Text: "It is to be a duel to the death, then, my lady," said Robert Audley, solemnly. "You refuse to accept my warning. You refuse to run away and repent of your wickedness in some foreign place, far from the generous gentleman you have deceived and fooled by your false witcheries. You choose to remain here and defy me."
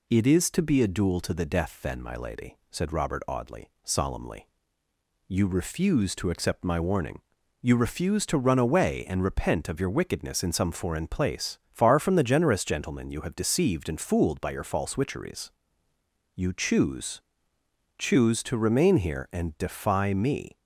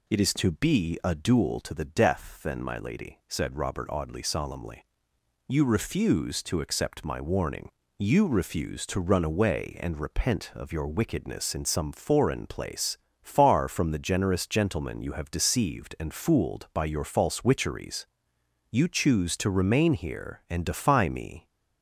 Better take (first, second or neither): second